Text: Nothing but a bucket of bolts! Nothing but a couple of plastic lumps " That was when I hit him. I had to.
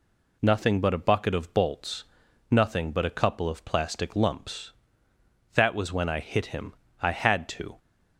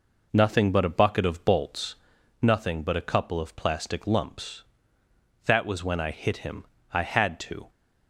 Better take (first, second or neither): first